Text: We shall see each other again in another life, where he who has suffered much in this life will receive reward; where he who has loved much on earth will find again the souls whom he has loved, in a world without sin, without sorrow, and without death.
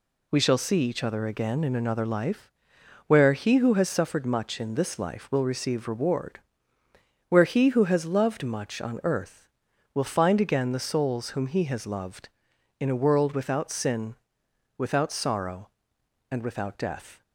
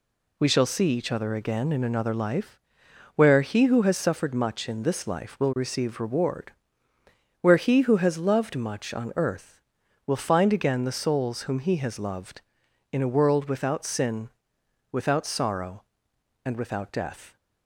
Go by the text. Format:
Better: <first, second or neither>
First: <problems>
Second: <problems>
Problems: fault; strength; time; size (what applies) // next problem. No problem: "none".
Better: neither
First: none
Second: none